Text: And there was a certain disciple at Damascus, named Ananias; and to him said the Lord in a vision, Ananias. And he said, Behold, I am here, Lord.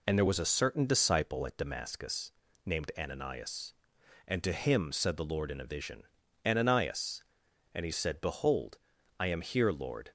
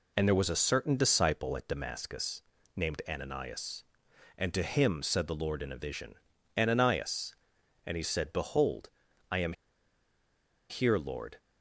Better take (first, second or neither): first